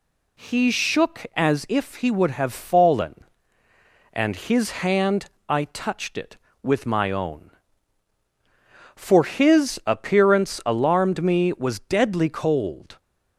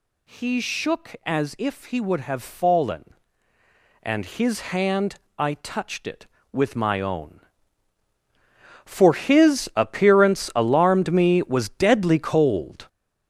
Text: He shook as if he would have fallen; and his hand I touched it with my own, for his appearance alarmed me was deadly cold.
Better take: first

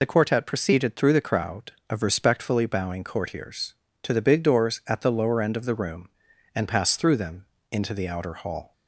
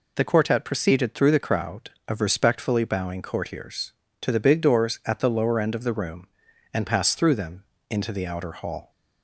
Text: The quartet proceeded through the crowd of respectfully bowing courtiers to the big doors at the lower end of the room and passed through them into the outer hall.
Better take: second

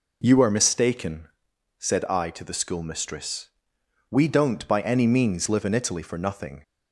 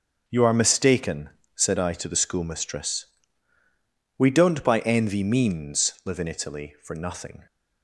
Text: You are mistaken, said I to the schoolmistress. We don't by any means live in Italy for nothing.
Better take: first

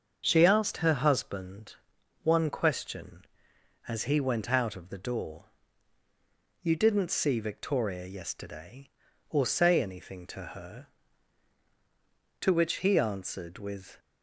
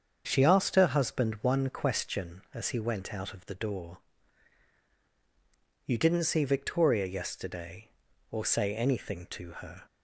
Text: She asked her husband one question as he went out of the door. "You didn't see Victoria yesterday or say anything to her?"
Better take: second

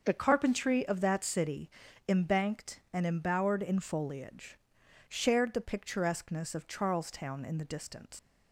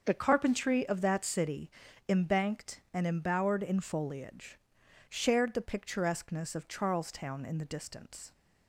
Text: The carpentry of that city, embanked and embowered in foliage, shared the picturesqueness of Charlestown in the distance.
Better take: second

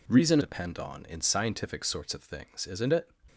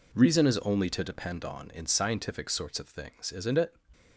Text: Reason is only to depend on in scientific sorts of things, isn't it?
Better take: second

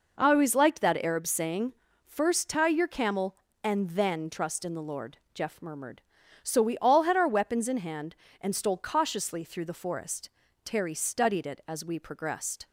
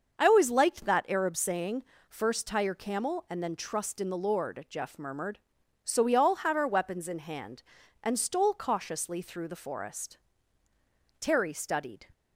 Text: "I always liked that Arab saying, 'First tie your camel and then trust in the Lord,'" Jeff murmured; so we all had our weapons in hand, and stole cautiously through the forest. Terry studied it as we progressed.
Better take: first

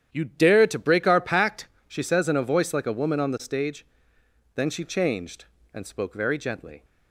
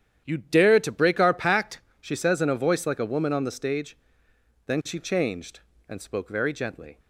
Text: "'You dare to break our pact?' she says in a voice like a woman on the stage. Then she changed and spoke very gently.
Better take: neither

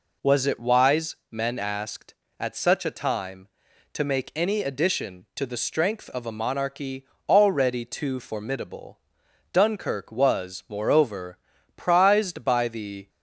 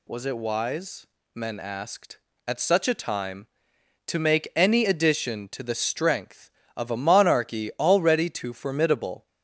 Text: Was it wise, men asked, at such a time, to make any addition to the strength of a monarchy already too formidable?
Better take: second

